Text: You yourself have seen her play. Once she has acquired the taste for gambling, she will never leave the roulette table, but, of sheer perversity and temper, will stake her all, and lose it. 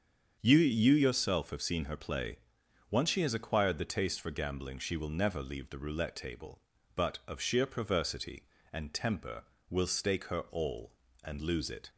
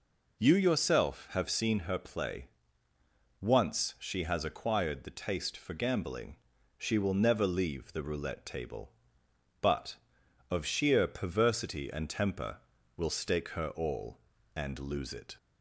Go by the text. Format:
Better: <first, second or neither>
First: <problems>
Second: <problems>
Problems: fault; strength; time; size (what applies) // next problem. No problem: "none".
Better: second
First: starts louder than the rest; strong; until 1.4 s; 7 dB // says "You" twice; at 0.5 s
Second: none